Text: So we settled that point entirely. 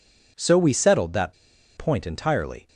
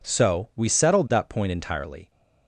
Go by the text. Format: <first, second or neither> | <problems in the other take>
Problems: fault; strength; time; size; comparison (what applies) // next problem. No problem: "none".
second | pauses between "that" and "point"; at 1.3 s; 0.42 s long